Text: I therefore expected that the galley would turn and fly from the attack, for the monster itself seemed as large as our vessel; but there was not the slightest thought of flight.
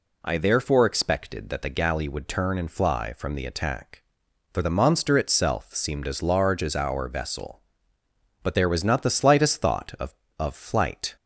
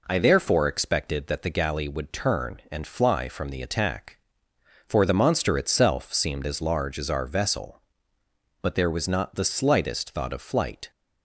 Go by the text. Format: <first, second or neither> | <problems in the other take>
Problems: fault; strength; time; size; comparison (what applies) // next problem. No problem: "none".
second | says "of" twice; at 10.3 s